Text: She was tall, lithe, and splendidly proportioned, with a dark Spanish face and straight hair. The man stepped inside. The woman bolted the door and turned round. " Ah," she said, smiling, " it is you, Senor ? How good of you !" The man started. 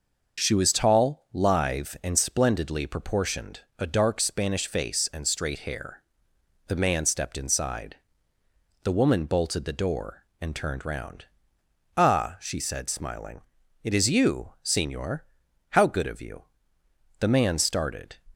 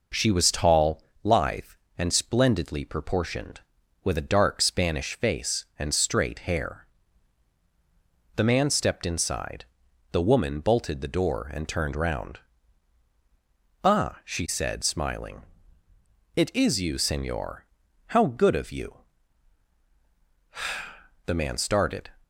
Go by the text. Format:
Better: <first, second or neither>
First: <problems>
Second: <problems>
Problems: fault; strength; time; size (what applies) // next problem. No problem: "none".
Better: second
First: skips "with"; at 3.6 s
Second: none